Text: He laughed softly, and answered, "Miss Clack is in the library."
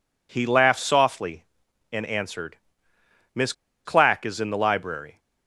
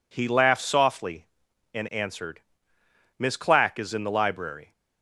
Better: second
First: pauses between "Miss" and "Clack"; slight; at 3.5 s; 0.33 s long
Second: none

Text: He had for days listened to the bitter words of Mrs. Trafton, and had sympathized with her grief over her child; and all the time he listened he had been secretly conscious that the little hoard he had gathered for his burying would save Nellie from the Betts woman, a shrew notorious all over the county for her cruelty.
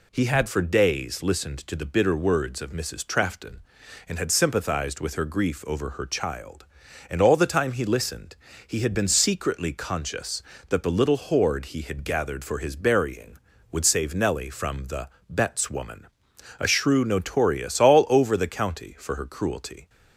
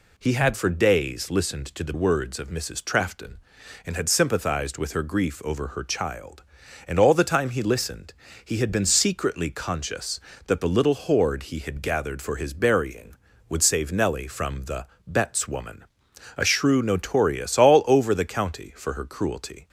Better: first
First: pauses between "listened" and "he"; slight; at 8.3 s; 0.32 s long // pauses between "the" and "Betts"; slight; at 15.0 s; 0.20 s long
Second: skips "bitter"; at 1.9 s // pauses between "listened" and "he"; slight; at 8.1 s; 0.32 s long // pauses between "the" and "Betts"; slight; at 14.8 s; 0.20 s long

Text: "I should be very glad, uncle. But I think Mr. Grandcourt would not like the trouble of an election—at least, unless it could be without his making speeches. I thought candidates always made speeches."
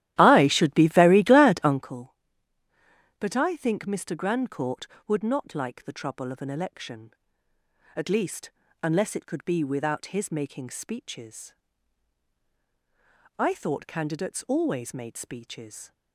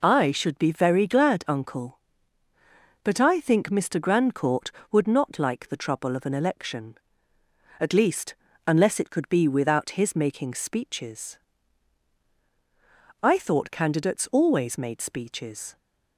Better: second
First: starts louder than the rest; strong; until 1.9 s; 13.5 dB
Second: none

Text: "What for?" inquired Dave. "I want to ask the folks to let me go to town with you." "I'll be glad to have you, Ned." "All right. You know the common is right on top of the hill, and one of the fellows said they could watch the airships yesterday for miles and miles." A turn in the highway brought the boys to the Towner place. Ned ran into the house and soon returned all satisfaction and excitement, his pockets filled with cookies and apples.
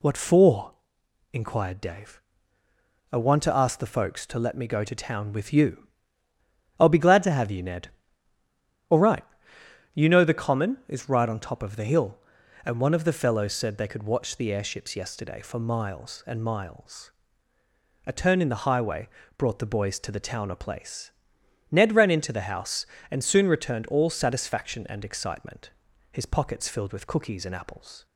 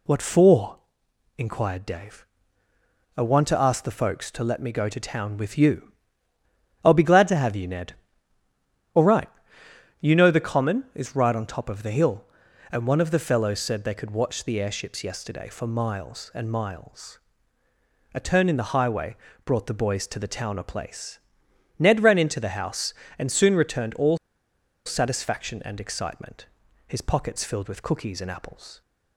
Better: first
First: pauses between "highway" and "brought"; slight; at 19.0 s; 0.28 s long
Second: pauses between "highway" and "brought"; slight; at 19.1 s; 0.28 s long // pauses between "all" and "satisfaction"; noticeable; at 24.1 s; 0.69 s long

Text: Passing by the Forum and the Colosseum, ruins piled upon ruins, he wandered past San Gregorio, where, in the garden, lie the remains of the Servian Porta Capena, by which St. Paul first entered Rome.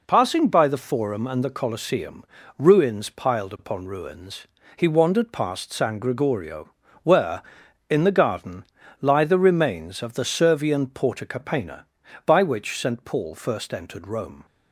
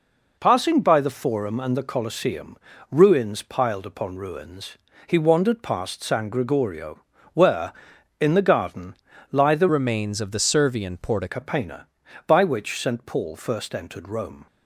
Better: first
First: none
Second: changes voice from "remains" to "Porta"; from 9.6 to 11.2 s; 1.6 s long

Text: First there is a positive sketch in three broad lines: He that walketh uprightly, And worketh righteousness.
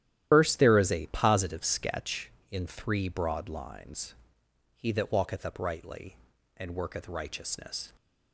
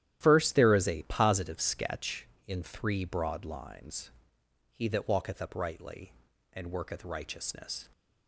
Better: second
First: loses the start of "First"; at 0.3 s; 75 ms // starts louder than the rest; strong; until 1.3 s; 12 dB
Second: starts louder than the rest; strong; until 1.2 s; 12.5 dB

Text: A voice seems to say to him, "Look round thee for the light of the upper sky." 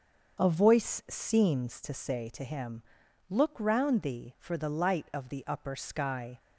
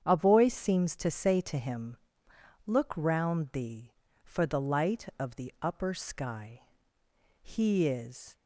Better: first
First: starts louder than the rest; until 1.4 s; 6.5 dB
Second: starts louder than the rest; strong; until 1.0 s; 8 dB // goes on to say "He is"; noticeable; from 7.4 s on; 0.94 s long

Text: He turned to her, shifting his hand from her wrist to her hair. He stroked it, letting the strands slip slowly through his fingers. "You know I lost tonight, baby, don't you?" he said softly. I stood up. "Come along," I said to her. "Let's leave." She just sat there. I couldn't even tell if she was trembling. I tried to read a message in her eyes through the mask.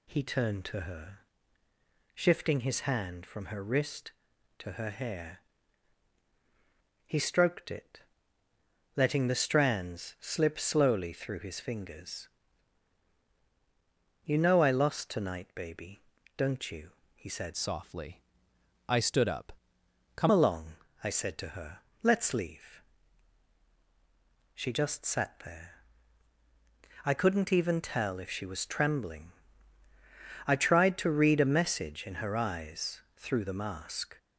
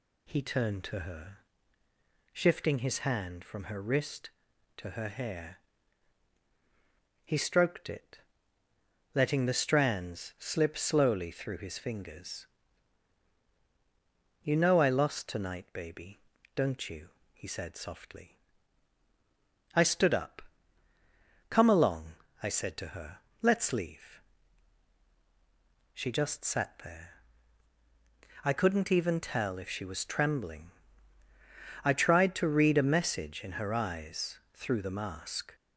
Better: second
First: changes voice from "softly" to "Come"; from 17.5 to 20.2 s; 2.7 s long // pauses between "eyes" and "through"; slight; at 32.9 s; 0.16 s long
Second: pauses between "eyes" and "through"; slight; at 34.3 s; 0.16 s long

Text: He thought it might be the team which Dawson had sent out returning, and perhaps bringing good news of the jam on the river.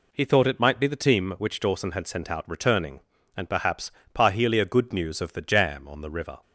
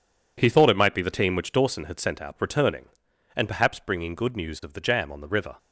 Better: second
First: says "parhelia" for "bringing"; at 4.1 s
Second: none

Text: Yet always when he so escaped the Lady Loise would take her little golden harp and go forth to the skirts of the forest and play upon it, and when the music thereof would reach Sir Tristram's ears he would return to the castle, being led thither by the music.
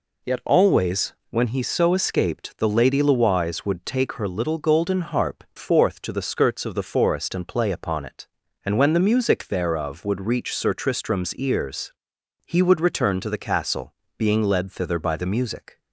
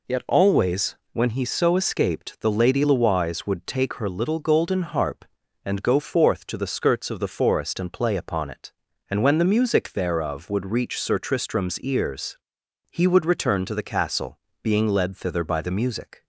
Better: second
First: pauses between "always" and "when"; slight; at 1.1 s; 0.16 s long // skips "and go"; at 5.5 s // pauses between "ears" and "he"; noticeable; at 11.9 s; 0.56 s long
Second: pauses between "always" and "when"; slight; at 0.9 s; 0.16 s long // pauses between "ears" and "he"; noticeable; at 12.3 s; 0.56 s long

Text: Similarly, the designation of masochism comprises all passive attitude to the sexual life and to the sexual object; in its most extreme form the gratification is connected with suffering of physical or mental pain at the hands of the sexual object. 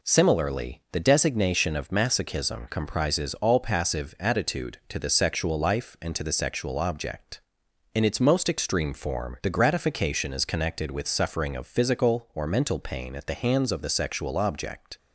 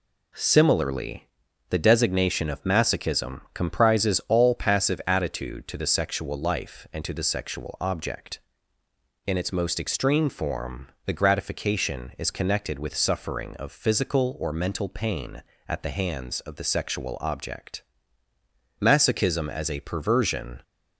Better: first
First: none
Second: pauses between "form" and "the"; slight; at 10.8 s; 0.18 s long // goes on to say "Masochism as a perversion"; strong; from 18.8 s on; 1.8 s long

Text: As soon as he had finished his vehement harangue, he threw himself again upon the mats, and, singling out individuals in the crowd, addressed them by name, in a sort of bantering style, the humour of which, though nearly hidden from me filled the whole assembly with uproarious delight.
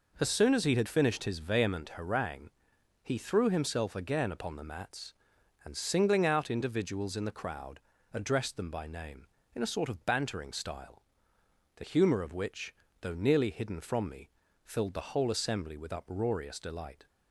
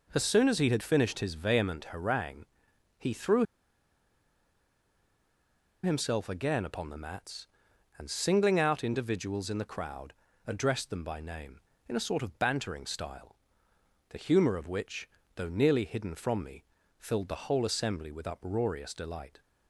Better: first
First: pauses between "me" and "filled"; slight; at 14.2 s; 0.36 s long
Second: pauses between "threw" and "himself"; strong; at 3.4 s; 2.3 s long // pauses between "me" and "filled"; slight; at 16.6 s; 0.36 s long

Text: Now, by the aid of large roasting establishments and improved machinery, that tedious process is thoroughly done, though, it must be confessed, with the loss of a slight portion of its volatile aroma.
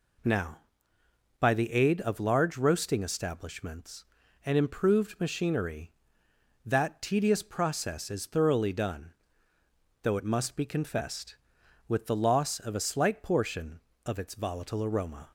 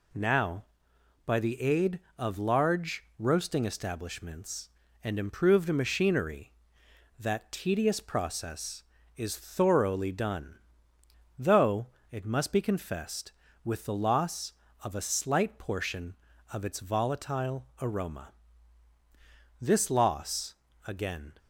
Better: first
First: none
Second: goes on to say "This loss again"; strong; from 19.6 s on; 1.7 s long

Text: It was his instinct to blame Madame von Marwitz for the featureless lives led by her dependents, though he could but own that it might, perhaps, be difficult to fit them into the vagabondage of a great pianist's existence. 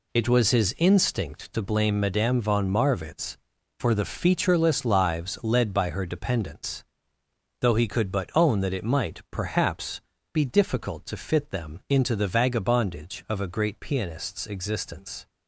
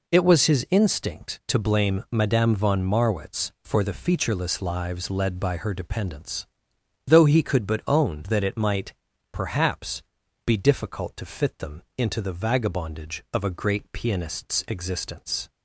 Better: neither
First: none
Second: none

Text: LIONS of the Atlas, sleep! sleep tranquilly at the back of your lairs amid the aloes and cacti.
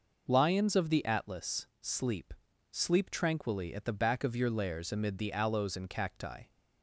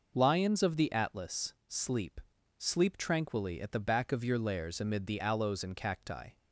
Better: neither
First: none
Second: none

